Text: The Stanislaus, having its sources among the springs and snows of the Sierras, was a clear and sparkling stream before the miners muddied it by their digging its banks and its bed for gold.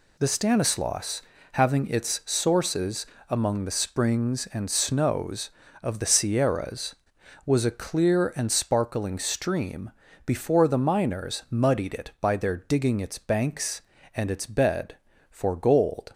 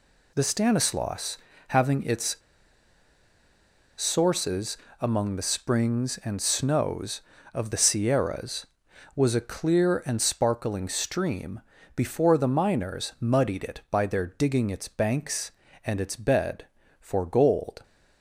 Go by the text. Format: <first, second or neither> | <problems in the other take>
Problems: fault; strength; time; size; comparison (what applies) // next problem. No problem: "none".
first | pauses between "its" and "sources"; strong; at 2.3 s; 1.6 s long // pauses between "sources" and "among"; slight; at 4.7 s; 0.22 s long; slight in the first // pauses between "stream" and "before"; slight; at 11.6 s; 0.34 s long; slight in the first